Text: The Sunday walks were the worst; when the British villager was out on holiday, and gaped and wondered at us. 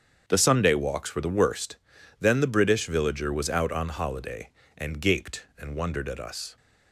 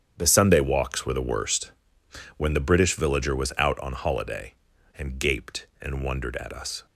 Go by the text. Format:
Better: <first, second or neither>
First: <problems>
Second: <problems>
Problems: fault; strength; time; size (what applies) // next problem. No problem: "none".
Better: second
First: starts louder than the rest; strong; until 1.2 s; 7.5 dB // says "then" for "when"; at 2.1 s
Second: starts louder than the rest; strong; until 1.1 s; 8 dB